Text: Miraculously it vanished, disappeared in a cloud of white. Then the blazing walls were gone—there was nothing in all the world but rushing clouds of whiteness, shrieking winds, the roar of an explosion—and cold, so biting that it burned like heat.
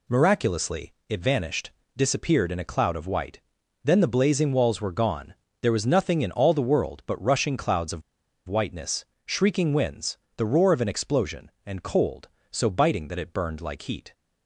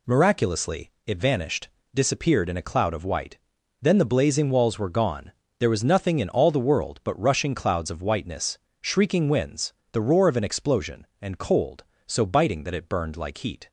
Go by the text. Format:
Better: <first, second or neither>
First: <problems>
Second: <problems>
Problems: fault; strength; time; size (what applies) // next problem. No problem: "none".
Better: second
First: pauses between "Miraculously" and "it"; slight; at 0.9 s; 0.16 s long // pauses between "of" and "whiteness"; noticeable; at 8.0 s; 0.47 s long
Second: pauses between "Miraculously" and "it"; slight; at 0.9 s; 0.16 s long